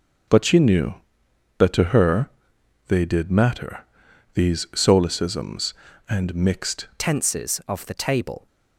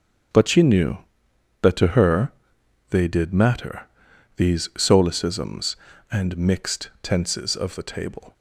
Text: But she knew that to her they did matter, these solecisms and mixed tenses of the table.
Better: second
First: starts louder than the rest; noticeable; until 1.9 s; 6 dB // pauses between "her" and "they"; noticeable; at 2.2 s; 0.58 s long // changes voice at "tenses"; from 6.9 s on; 1.5 s long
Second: starts louder than the rest; strong; until 1.9 s; 7.5 dB // pauses between "her" and "they"; noticeable; at 2.3 s; 0.58 s long

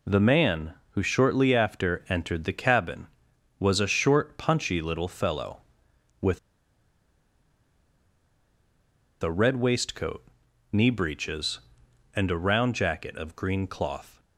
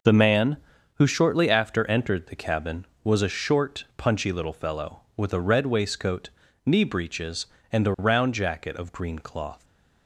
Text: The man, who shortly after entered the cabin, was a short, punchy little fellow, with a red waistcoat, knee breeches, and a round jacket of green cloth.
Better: second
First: pauses between "with" and "a"; strong; at 6.3 s; 2.8 s long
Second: none

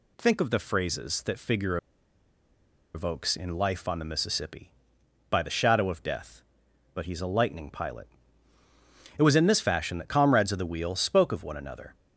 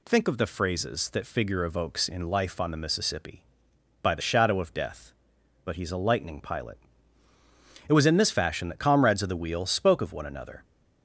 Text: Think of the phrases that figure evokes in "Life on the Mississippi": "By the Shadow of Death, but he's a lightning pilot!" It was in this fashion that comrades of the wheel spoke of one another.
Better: second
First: pauses between "figure" and "evokes"; at 1.7 s; 1.1 s long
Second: none

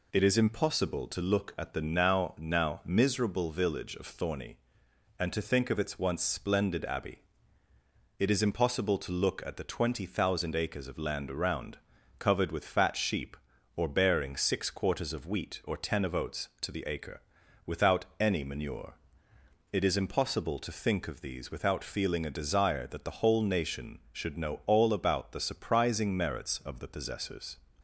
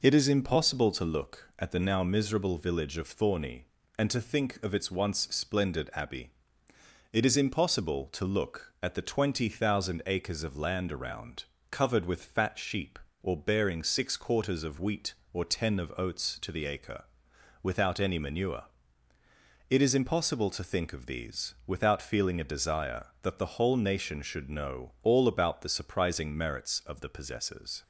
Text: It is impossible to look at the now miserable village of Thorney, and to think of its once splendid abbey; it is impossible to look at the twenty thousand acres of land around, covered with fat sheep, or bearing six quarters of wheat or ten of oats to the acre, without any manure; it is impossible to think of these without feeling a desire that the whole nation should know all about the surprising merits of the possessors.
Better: second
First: says "now" twice; at 2.3 s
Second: none

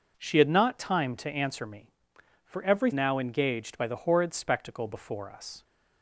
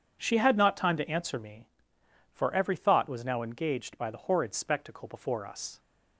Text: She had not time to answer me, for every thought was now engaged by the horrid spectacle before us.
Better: second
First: skips "thought was"; at 2.9 s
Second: none

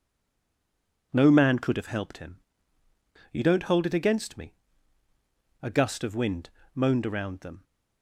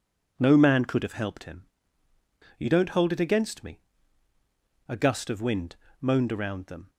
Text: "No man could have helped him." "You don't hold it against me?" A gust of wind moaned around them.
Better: second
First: stays silent before the first word; until 1.1 s; 1.1 s long // pauses between "wind" and "moaned"; slight; at 6.5 s; 0.24 s long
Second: pauses between "wind" and "moaned"; slight; at 5.7 s; 0.24 s long

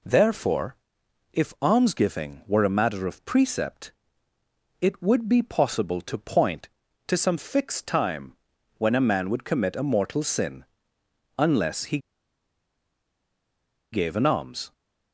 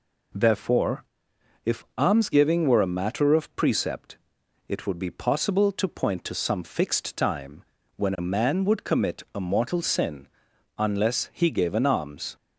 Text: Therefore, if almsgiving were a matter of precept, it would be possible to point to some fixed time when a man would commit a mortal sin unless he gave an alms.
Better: second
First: pauses between "time" and "when"; noticeable; at 8.3 s; 0.46 s long // pauses between "sin" and "unless"; noticeable; at 10.6 s; 0.72 s long // pauses between "he" and "gave"; strong; at 11.9 s; 1.9 s long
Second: pauses between "time" and "when"; slight; at 7.6 s; 0.32 s long // pauses between "sin" and "unless"; noticeable; at 10.2 s; 0.50 s long

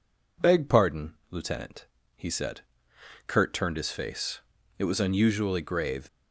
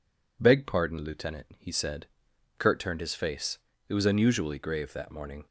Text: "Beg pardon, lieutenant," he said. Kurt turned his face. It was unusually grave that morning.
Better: second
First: stops before "that morning"; at 6.0 s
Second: none

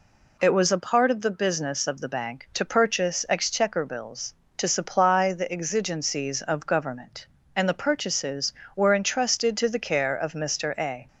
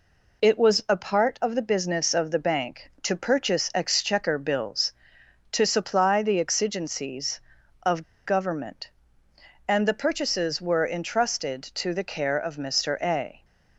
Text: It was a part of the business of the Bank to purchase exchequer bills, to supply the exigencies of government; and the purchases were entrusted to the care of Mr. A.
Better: first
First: none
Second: pauses between "of" and "government"; slight; at 8.0 s; 0.21 s long

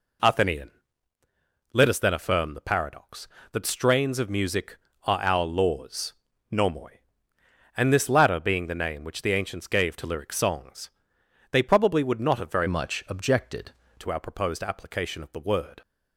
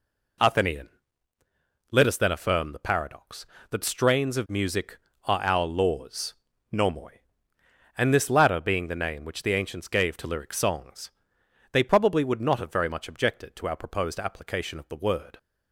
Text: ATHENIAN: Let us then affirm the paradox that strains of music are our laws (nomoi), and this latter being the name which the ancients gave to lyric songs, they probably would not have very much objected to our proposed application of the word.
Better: second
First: changes voice from "much" to "objected"; from 12.6 to 13.7 s; 1.1 s long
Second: none

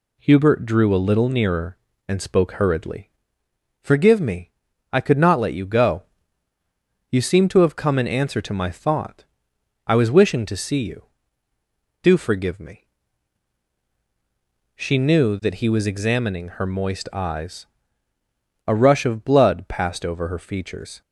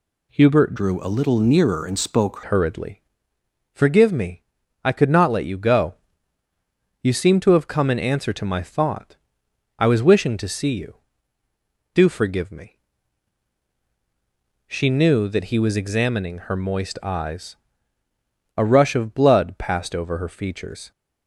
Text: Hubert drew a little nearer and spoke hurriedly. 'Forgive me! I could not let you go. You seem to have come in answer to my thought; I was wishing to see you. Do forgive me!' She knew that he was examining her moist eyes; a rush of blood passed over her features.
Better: first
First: none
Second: changes voice from "drew" to "spoke"; from 0.7 to 2.3 s; 1.6 s long

